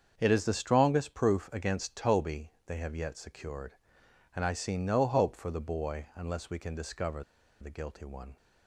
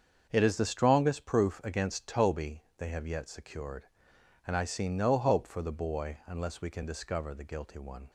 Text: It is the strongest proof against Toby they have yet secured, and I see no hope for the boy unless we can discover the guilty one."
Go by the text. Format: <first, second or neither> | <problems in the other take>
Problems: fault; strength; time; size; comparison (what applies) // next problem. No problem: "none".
second | starts louder than the rest; until 1.1 s; 7 dB; also in the second // pauses between "Toby" and "they"; slight; at 2.4 s; 0.18 s long; slight in the second // pauses between "discover" and "the"; at 7.2 s; 0.38 s long